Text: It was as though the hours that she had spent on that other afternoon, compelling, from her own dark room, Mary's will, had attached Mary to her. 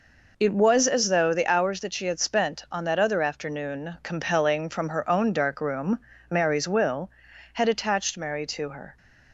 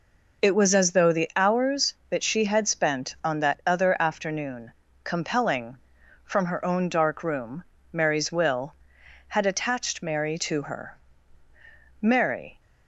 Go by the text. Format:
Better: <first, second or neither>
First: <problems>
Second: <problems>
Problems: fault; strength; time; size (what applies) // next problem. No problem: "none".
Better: first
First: none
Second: goes on to say "Mary"; from 12.0 s on; 0.58 s long